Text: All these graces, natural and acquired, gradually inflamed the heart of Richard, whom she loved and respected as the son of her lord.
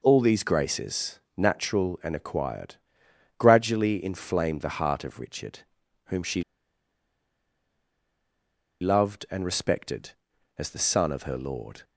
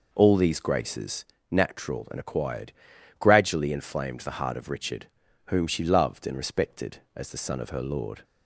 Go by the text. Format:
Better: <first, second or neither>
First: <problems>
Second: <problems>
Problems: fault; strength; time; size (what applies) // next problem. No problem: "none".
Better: second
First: pauses between "she" and "loved"; strong; at 6.4 s; 2.3 s long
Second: none